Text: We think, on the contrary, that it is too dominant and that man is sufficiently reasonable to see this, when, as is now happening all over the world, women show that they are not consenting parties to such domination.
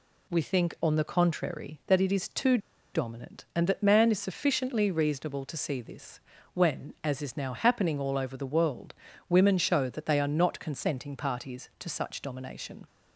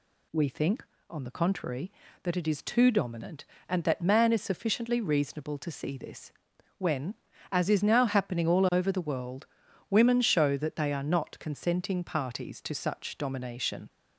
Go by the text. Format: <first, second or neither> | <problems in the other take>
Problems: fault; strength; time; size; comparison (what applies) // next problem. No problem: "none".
second | pauses between "too" and "dominant"; slight; at 2.5 s; 0.35 s long